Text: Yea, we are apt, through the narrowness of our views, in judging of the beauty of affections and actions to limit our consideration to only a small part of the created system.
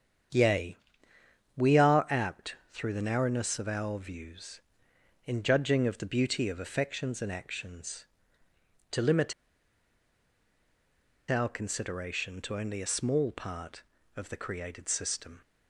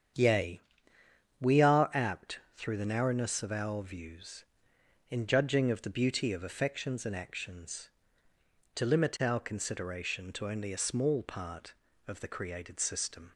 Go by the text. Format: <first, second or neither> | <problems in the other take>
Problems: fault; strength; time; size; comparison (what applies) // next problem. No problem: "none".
second | starts louder than the rest; strong; until 2.1 s; 8 dB; strong in the second // pauses between "limit" and "our"; strong; at 9.3 s; 1.9 s long